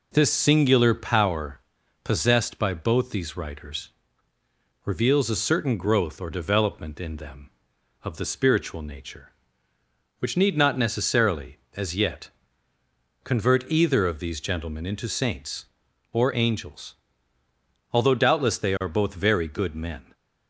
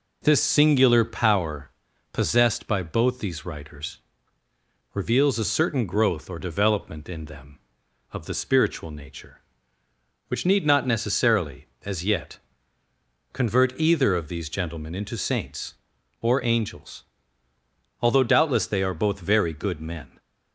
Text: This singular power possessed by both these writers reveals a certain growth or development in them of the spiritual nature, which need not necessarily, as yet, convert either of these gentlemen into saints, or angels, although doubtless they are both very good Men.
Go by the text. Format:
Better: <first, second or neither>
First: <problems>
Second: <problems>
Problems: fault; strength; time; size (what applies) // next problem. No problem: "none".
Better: neither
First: pauses between "power" and "possessed"; at 1.6 s; 0.42 s long // pauses between "writers" and "reveals"; noticeable; at 3.8 s; 0.96 s long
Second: pauses between "power" and "possessed"; at 1.7 s; 0.40 s long // pauses between "writers" and "reveals"; noticeable; at 3.9 s; 0.96 s long